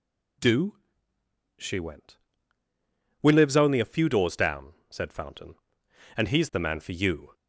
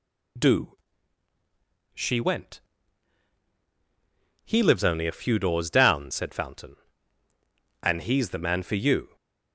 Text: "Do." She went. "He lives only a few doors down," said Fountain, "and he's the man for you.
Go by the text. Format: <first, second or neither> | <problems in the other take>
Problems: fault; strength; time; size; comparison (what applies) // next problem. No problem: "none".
second | says "We" for "He"; at 3.2 s